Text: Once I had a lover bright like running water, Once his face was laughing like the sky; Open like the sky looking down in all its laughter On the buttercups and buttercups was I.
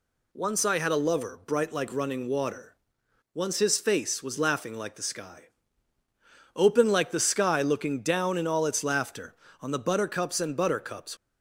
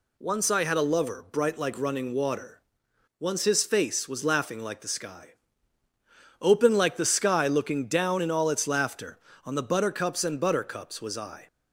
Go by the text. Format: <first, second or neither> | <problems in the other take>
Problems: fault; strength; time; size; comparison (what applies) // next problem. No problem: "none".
second | stops before "was I"; at 11.1 s